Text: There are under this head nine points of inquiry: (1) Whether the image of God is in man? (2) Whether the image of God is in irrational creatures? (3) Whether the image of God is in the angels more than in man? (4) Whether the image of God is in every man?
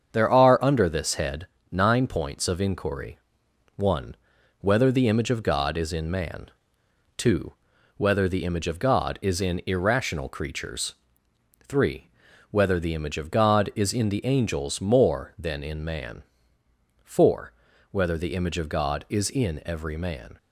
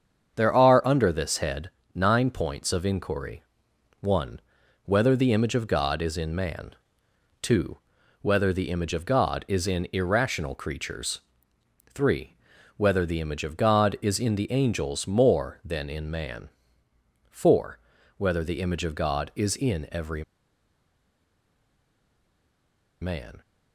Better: first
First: starts louder than the rest; strong; until 1.1 s; 7 dB // pauses between "head" and "nine"; slight; at 1.4 s; 0.24 s long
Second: starts louder than the rest; strong; until 1.4 s; 7 dB // pauses between "head" and "nine"; slight; at 1.6 s; 0.24 s long // pauses between "every" and "man"; strong; at 20.2 s; 2.7 s long

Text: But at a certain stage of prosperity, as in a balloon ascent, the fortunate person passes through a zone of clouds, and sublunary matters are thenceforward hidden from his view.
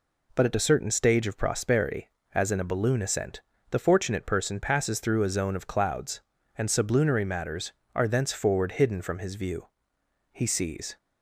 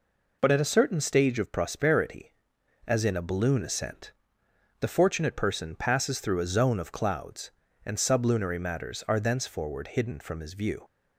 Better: second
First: goes on to say "He sees"; noticeable; from 10.3 s on; 0.64 s long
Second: none

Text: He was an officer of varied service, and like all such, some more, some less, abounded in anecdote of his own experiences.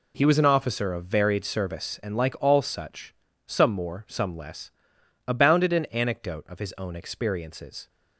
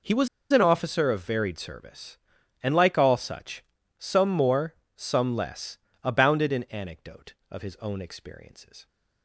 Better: first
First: none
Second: pauses between "was" and "an"; slight; at 0.2 s; 0.24 s long

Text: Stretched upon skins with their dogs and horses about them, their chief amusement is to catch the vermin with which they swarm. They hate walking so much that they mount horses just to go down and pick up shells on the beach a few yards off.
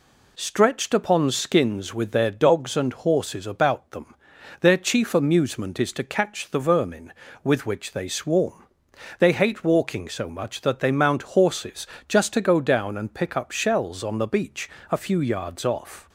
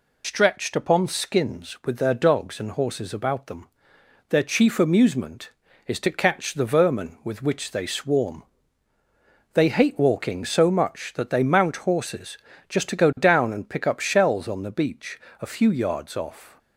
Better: first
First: pauses between "horses" and "just"; slight; at 11.8 s; 0.24 s long // pauses between "beach" and "a"; slight; at 14.6 s; 0.22 s long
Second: loses the start of "Stretched"; at 0.2 s; 100 ms // pauses between "horses" and "just"; slight; at 12.3 s; 0.30 s long // pauses between "beach" and "a"; slight; at 15.1 s; 0.20 s long

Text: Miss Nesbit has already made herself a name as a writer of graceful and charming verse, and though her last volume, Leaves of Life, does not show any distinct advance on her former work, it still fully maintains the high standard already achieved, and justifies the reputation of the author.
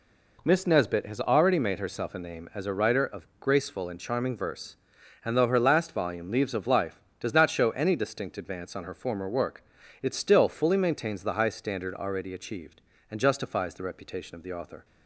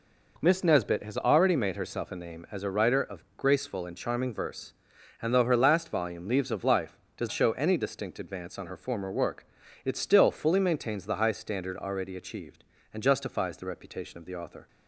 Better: first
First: none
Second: skips "not"; at 7.3 s

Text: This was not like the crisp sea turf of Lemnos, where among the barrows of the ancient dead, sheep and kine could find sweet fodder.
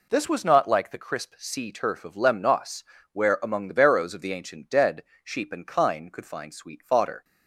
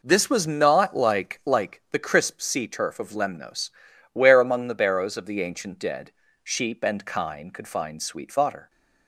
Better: first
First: none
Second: says "like" twice; at 1.4 s

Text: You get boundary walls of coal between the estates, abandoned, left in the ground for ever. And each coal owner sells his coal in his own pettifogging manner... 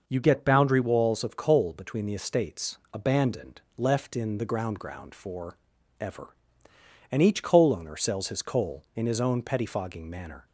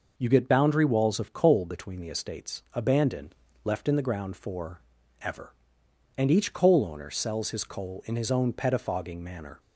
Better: second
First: says "ground" twice; at 4.7 s // pauses between "for" and "ever"; at 5.5 s; 0.42 s long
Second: pauses between "for" and "ever"; at 4.7 s; 0.42 s long

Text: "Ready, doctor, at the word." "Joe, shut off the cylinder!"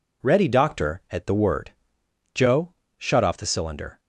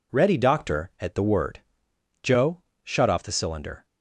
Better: neither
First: none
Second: none

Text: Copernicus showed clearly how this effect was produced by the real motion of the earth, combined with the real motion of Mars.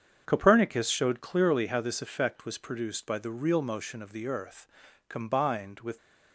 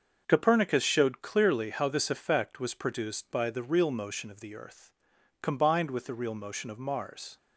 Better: second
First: starts louder than the rest; strong; until 1.2 s; 7.5 dB // stops before "the real motion of Mars"; at 5.9 s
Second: starts louder than the rest; until 1.2 s; 6.5 dB

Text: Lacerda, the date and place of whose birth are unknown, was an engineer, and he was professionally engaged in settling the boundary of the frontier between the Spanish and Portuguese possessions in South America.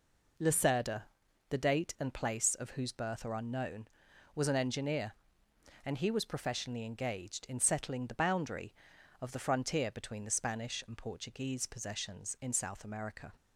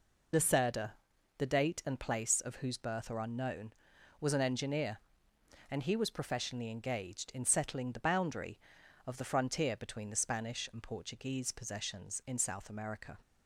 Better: first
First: none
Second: loses the start of "Lacerda"; at 0.3 s; 65 ms

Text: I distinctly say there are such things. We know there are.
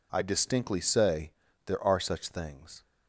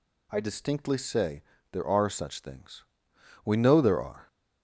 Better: second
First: pauses between "say" and "there"; slight; at 1.3 s; 0.34 s long // stops before "We know there are"; at 2.8 s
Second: pauses between "say" and "there"; slight; at 1.4 s; 0.30 s long

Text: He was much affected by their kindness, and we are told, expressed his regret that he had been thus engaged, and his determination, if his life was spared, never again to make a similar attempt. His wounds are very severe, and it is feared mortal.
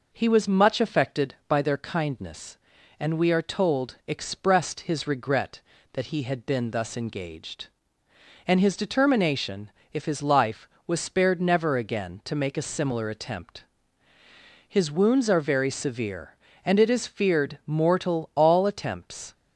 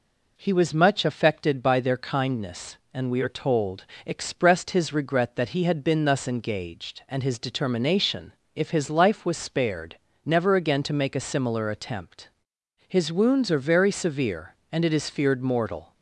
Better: second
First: goes on to say "All attempts"; noticeable; from 18.3 s on; 0.98 s long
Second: none

